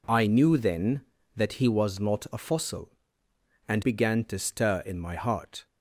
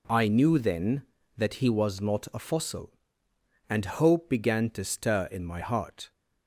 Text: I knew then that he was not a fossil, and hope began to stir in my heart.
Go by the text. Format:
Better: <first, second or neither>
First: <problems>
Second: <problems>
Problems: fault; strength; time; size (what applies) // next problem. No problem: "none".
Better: second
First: skips "hope"; at 3.8 s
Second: none